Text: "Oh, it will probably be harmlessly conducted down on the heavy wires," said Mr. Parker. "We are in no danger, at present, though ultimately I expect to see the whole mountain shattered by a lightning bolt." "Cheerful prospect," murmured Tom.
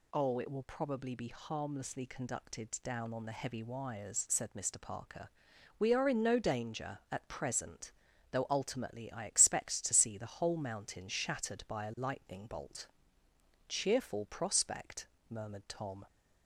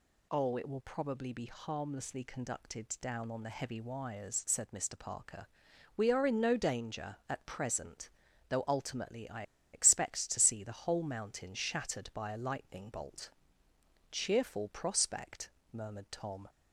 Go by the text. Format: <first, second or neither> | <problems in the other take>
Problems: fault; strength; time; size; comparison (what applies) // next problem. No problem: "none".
first | pauses between "I" and "expect"; slight; at 9.4 s; 0.30 s long